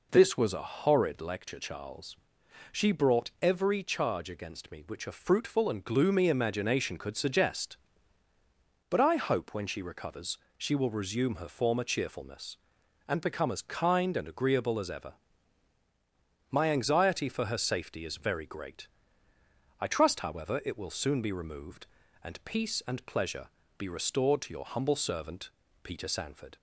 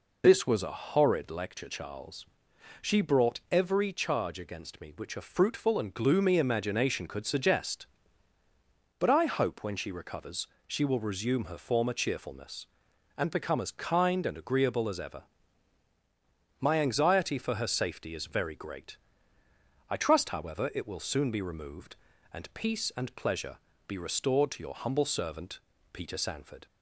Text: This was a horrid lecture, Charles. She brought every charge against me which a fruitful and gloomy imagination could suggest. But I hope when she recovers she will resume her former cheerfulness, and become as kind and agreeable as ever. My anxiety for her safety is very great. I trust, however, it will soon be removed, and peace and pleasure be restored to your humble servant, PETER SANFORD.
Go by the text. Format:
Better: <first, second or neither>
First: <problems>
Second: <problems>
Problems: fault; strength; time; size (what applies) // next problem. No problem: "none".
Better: first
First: pauses between "recovers" and "she"; slight; at 10.3 s; 0.22 s long // pauses between "pleasure" and "be"; slight; at 23.4 s; 0.32 s long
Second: loses the start of "This"; at 0.2 s; 45 ms // pauses between "recovers" and "she"; slight; at 10.4 s; 0.22 s long // pauses between "pleasure" and "be"; slight; at 23.5 s; 0.32 s long